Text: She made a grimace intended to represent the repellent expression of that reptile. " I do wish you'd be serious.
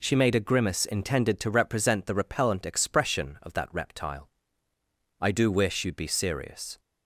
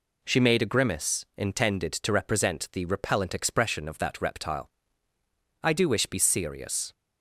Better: first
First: none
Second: skips "you'd"; at 6.0 s

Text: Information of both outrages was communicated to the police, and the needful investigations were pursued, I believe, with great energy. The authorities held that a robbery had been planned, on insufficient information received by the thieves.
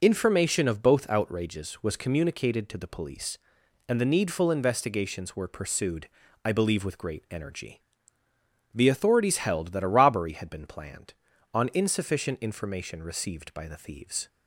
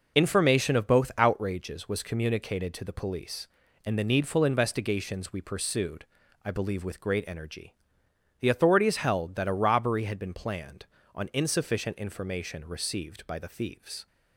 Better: first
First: none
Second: says "we" for "were"; at 5.3 s

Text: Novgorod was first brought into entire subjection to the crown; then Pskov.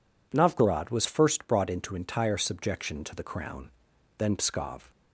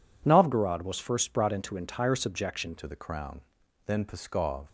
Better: first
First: none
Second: changes voice at "to"; from 2.7 s on; 1.9 s long

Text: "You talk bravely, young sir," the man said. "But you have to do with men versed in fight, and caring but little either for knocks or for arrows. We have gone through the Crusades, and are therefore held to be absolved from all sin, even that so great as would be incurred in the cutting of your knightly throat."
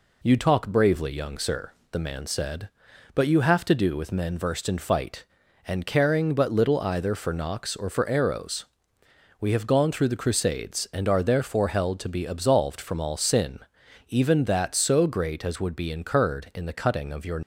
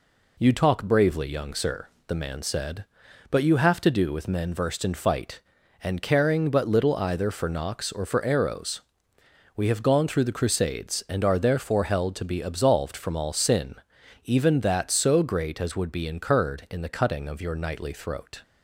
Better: second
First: stops before "knightly throat"; at 17.4 s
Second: none

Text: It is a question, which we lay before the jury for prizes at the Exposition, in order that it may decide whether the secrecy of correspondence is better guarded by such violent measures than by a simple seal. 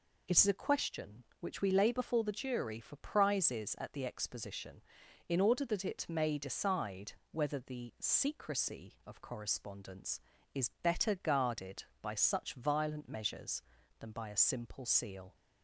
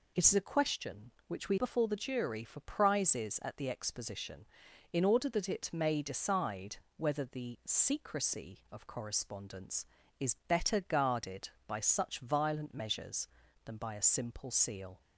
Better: first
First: pauses between "decide" and "whether"; slight; at 7.1 s; 0.18 s long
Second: skips "lay"; at 1.5 s // pauses between "decide" and "whether"; slight; at 6.7 s; 0.20 s long

